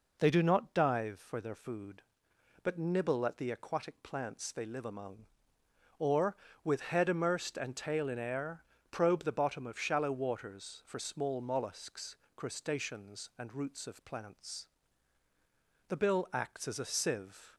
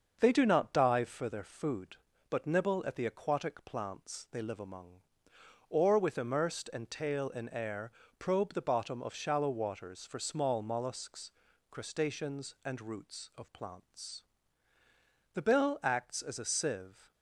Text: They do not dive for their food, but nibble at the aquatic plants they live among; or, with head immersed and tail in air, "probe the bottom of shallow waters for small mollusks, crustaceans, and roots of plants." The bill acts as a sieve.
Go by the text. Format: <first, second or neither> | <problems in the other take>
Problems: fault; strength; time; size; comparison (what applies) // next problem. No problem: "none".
first | starts louder than the rest; until 1.2 s; 6.5 dB // skips "head"; at 6.1 s